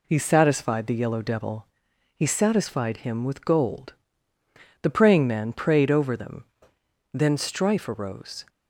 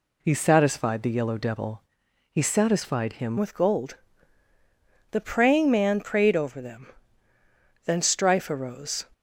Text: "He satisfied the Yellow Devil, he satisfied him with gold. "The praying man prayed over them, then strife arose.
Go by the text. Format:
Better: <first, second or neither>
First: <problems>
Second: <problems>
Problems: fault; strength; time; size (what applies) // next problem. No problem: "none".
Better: first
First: none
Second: changes voice at "with"; from 3.3 s on; 5.7 s long